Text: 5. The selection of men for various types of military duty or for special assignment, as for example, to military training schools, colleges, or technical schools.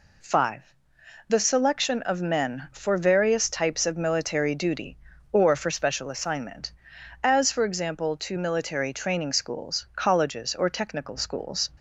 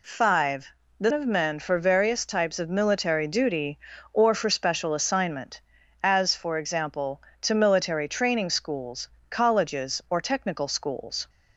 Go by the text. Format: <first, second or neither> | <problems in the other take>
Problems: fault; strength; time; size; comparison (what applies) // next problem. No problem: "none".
first | skips "selection"; at 1.1 s